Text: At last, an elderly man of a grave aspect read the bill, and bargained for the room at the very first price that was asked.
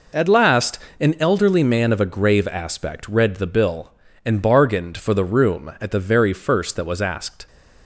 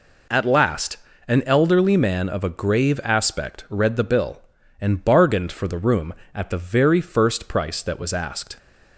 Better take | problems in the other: second | skips "price"; at 6.7 s

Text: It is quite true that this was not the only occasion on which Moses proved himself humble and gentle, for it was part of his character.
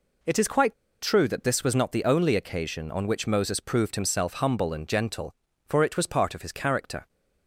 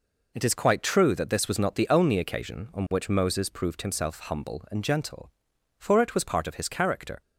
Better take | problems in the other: second | pauses between "quite" and "true"; slight; at 0.7 s; 0.28 s long

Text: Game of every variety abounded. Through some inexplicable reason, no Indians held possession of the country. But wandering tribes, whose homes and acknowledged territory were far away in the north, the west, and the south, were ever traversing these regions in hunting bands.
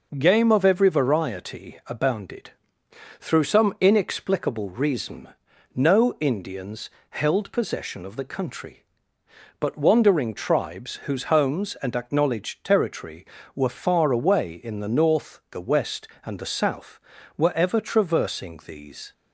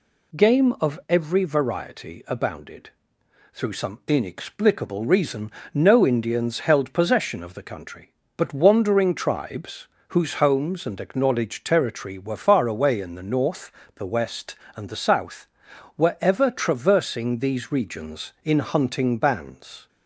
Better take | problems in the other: second | pauses between "Indians" and "held"; slight; at 6.8 s; 0.22 s long // stops before "regions in hunting bands"; at 19.1 s

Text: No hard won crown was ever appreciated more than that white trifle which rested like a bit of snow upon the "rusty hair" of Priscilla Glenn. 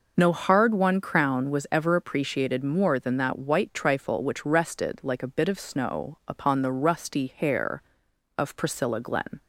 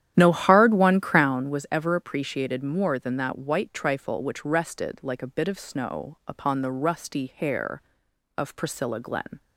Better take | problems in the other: first | starts louder than the rest; strong; until 1.4 s; 11 dB

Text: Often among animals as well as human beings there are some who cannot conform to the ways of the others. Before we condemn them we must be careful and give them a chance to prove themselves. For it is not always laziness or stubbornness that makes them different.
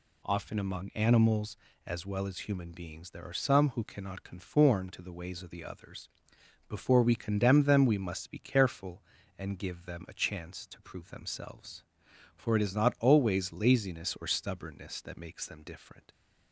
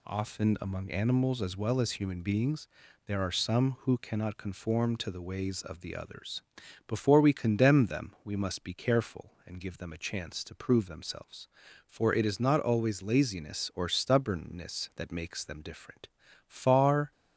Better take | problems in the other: first | pauses between "beings" and "there"; at 2.6 s; 0.40 s long // goes on to say "Far"; noticeable; from 16.4 s on; 0.64 s long

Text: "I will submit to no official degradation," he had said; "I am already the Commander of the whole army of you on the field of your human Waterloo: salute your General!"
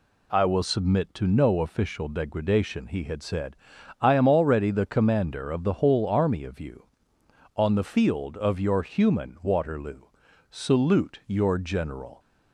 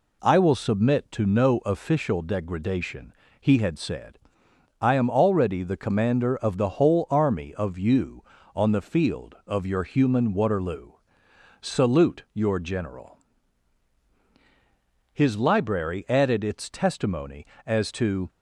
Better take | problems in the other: first | goes on to say "His library added its testimony as to"; strong; from 15.1 s on; 3.1 s long

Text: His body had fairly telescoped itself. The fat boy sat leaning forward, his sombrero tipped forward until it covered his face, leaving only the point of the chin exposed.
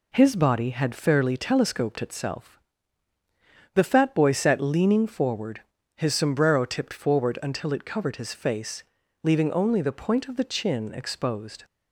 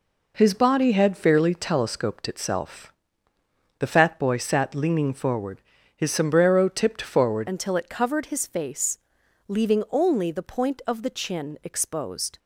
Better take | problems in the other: first | changes voice at "until"; from 7.4 s on; 4.9 s long

